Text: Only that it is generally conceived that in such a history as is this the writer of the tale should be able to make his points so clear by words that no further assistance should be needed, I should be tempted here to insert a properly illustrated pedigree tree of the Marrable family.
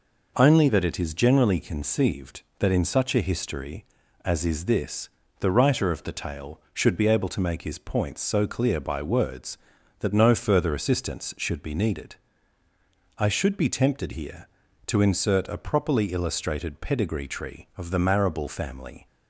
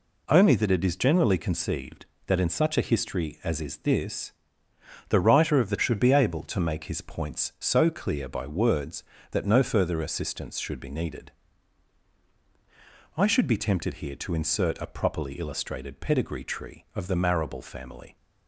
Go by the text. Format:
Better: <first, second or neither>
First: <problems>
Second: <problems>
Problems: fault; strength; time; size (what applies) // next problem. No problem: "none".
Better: first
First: pauses between "this" and "the"; slight; at 5.0 s; 0.32 s long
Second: pauses between "this" and "the"; noticeable; at 4.3 s; 0.78 s long // skips "tale"; at 5.7 s